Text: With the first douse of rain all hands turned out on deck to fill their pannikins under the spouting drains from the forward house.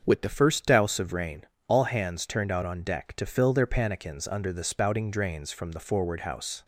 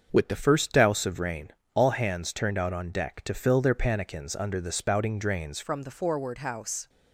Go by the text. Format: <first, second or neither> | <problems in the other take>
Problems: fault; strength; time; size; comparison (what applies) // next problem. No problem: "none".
first | starts louder than the rest; until 1.1 s; 6.5 dB; also in the first // pauses between "rain" and "all"; slight; at 1.5 s; 0.22 s long; slight in the first // changes voice at "from"; from 5.6 s on; 1.2 s long